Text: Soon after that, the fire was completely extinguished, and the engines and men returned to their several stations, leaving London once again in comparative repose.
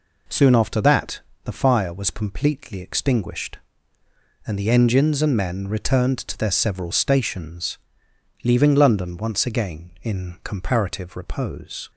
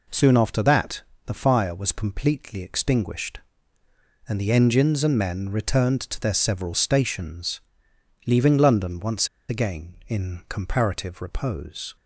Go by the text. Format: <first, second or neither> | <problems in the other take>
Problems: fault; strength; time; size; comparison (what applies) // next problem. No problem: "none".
first | pauses between "once" and "again"; slight; at 9.2 s; 0.21 s long